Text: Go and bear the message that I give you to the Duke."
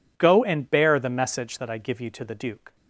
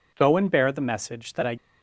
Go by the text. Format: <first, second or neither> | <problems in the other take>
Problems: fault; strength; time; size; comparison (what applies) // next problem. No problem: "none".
first | stops before "give you to the Duke"; at 1.5 s